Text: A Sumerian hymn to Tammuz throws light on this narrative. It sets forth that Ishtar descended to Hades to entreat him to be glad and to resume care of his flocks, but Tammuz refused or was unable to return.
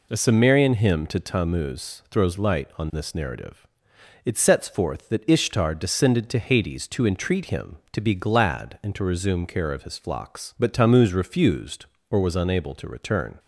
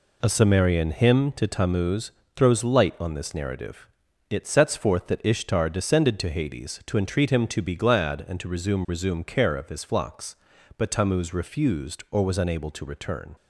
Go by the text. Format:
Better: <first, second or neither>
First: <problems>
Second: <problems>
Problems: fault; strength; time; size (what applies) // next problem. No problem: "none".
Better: first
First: none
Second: pauses between "Tammuz" and "throws"; slight; at 2.1 s; 0.24 s long // says "resume" twice; at 8.8 s